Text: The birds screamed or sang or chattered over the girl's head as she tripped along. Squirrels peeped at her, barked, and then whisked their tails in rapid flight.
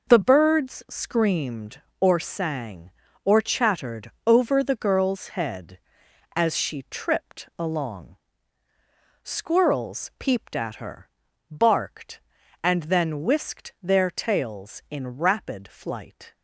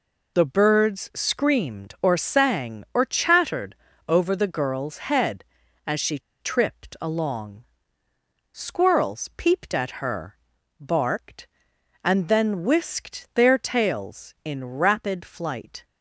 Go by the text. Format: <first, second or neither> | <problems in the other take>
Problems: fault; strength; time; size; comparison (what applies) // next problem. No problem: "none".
first | pauses between "chattered" and "over"; slight; at 3.7 s; 0.32 s long // pauses between "she" and "tripped"; slight; at 6.1 s; 0.21 s long